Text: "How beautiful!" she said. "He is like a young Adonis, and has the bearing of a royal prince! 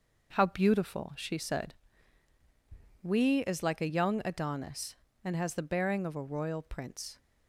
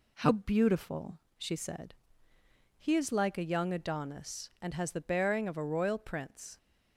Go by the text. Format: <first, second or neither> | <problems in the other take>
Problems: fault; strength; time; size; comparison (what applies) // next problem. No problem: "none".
second | says "We" for "He"; at 3.0 s